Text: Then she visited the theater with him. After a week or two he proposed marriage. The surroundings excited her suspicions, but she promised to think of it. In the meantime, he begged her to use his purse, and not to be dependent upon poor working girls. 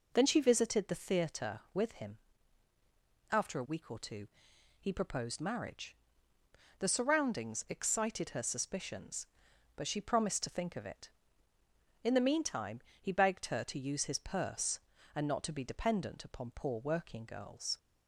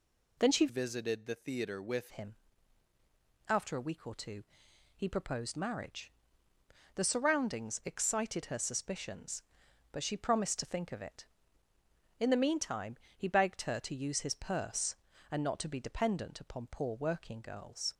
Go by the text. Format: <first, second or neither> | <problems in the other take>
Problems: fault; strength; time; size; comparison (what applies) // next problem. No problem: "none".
first | changes voice from "visited" to "with"; from 0.6 to 2.1 s; 1.5 s long // pauses between "two" and "he"; noticeable; at 4.4 s; 0.52 s long; noticeable in the first